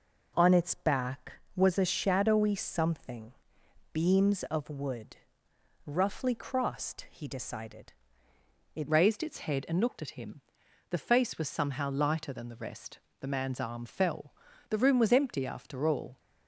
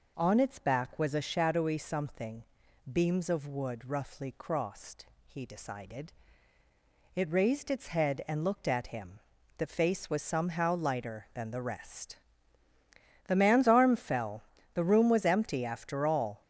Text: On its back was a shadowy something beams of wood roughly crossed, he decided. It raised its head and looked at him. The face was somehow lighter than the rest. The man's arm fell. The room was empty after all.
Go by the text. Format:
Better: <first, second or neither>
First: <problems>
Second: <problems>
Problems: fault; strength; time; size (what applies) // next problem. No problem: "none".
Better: second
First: pauses between "something" and "beams"; noticeable; at 3.3 s; 0.58 s long // pauses between "wood" and "roughly"; noticeable; at 5.1 s; 0.68 s long // changes voice at "raised"; from 8.8 s on; 7.3 s long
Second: pauses between "something" and "beams"; noticeable; at 2.4 s; 0.49 s long